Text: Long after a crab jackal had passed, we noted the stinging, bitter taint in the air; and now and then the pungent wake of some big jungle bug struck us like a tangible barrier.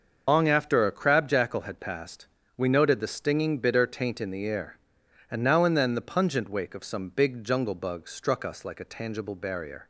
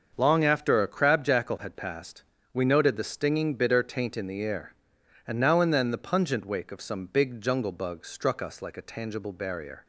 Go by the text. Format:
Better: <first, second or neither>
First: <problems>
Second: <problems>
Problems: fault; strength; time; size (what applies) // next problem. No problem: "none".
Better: second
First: loses the start of "Long"; at 0.2 s; 100 ms // starts louder than the rest; until 1.2 s; 6.5 dB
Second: starts louder than the rest; until 1.1 s; 6.5 dB